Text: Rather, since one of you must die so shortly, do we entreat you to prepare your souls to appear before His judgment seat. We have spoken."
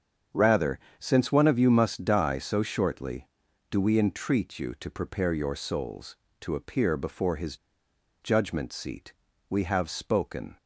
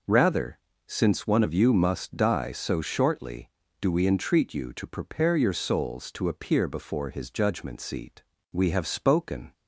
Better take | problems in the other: second | starts louder than the rest; strong; until 1.5 s; 7.5 dB // pauses between "His" and "judgment"; noticeable; at 7.5 s; 0.66 s long

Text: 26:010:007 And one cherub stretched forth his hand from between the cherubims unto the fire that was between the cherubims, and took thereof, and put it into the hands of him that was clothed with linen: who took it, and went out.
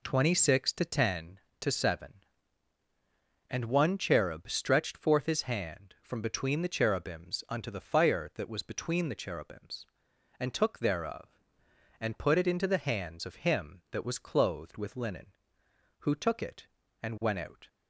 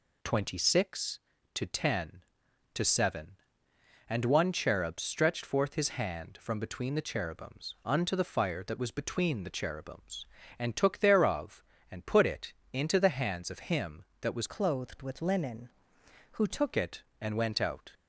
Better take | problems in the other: first | pauses between "it" and "into"; slight; at 12.5 s; 0.18 s long // changes voice from "clothed" to "took"; from 14.4 to 16.7 s; 2.3 s long

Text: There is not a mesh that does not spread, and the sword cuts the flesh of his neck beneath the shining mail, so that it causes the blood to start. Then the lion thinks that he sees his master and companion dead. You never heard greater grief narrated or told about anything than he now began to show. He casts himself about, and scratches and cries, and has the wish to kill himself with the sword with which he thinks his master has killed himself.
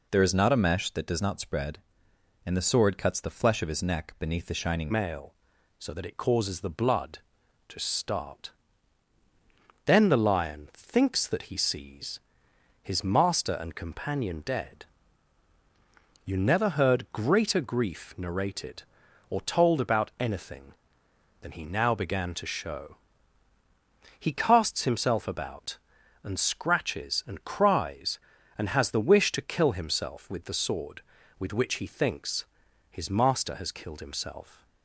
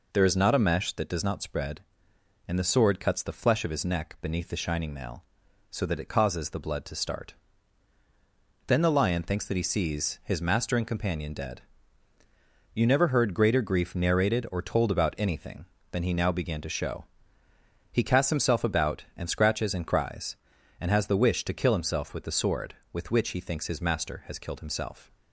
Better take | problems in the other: second | changes voice at "mail"; from 4.9 s on; 29.7 s long // pauses between "sees" and "his"; noticeable; at 12.1 s; 0.64 s long // pauses between "thinks" and "his"; noticeable; at 32.4 s; 0.46 s long

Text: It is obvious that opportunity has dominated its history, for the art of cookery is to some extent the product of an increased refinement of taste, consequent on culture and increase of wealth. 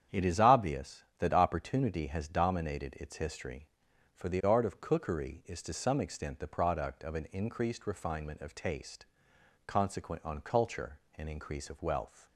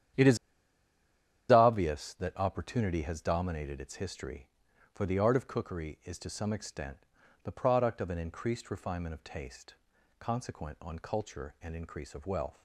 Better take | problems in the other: first | starts louder than the rest; strong; until 2.3 s; 10 dB; strong in the first // pauses between "is" and "obvious"; at 0.3 s; 1.1 s long // pauses between "extent" and "the"; at 6.9 s; 0.44 s long

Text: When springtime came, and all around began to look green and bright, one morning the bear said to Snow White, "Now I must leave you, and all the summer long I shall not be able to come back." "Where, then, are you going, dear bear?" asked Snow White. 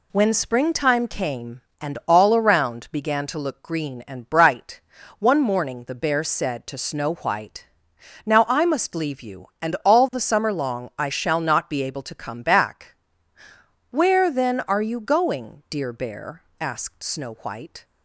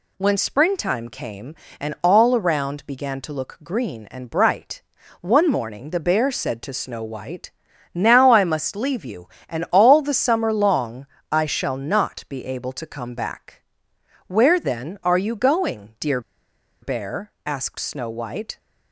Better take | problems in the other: first | pauses between "long" and "I"; slight; at 11.0 s; 0.24 s long // pauses between "dear" and "bear"; noticeable; at 16.2 s; 0.62 s long

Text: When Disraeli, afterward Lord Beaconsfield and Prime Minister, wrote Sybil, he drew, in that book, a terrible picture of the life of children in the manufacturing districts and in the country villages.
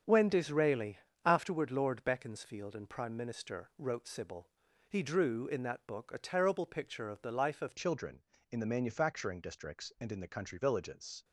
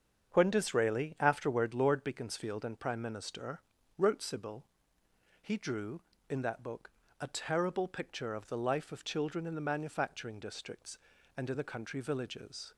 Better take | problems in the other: second | starts louder than the rest; until 1.3 s; 7 dB; strong in the second // changes voice at "children"; from 7.7 s on; 3.5 s long

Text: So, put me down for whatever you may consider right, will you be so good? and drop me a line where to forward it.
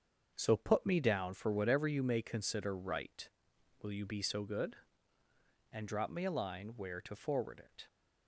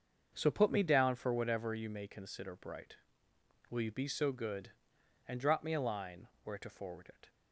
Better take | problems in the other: first | starts louder than the rest; until 1.3 s; 6.5 dB; also in the first // says "bright" for "right"; at 2.5 s // pauses between "line" and "where"; slight; at 6.2 s; 0.16 s long

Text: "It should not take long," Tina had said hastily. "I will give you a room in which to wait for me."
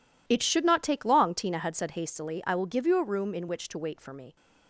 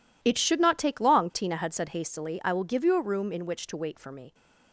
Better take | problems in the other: neither | none

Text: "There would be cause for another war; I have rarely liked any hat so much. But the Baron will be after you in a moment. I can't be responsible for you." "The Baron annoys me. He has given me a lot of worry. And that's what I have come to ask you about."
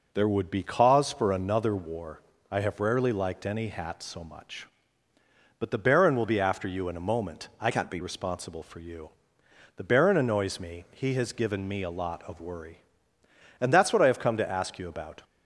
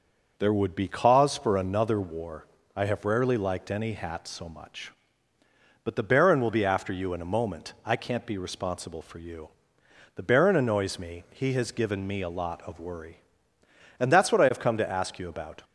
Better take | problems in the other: second | changes voice from "can't" to "be"; from 7.7 to 7.9 s; 0.2 s long

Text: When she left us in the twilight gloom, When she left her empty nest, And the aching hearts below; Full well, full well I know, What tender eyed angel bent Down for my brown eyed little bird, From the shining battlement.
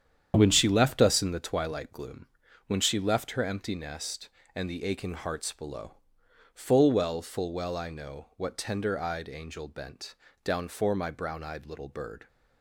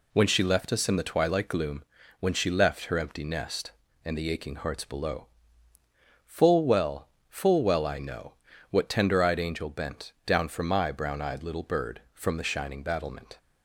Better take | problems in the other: second | starts louder than the rest; strong; until 1.3 s; 8.5 dB // pauses between "bent" and "Down"; slight; at 10.1 s; 0.28 s long // stops before "From the shining battlement"; at 12.2 s

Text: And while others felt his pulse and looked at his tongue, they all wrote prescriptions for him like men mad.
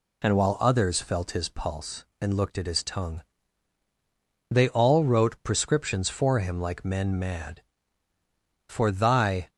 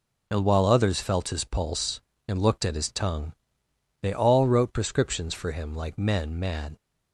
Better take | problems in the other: second | goes on to say "For thy"; noticeable; from 8.6 s on; 0.80 s long

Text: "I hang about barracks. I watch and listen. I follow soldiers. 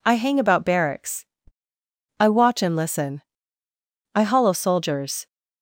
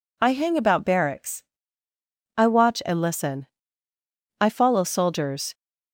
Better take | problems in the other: second | says "hollow" for "follow"; at 4.2 s

